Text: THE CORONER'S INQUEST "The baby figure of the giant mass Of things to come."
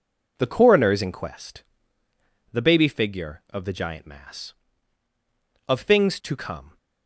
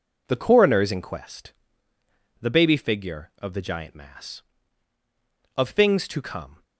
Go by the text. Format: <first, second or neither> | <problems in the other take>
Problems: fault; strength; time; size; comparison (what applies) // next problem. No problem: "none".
neither | pauses between "INQUEST" and "The"; noticeable; the same in both